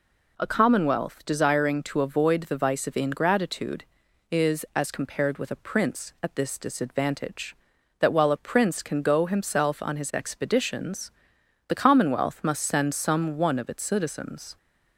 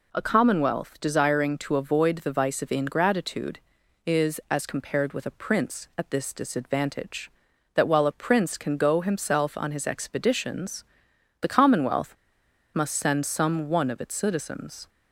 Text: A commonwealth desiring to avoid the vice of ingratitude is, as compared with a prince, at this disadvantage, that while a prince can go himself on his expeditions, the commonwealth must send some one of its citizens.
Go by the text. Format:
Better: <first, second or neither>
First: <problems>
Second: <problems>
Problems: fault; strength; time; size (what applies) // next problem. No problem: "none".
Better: first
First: none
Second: pauses between "commonwealth" and "must"; noticeable; at 12.1 s; 0.59 s long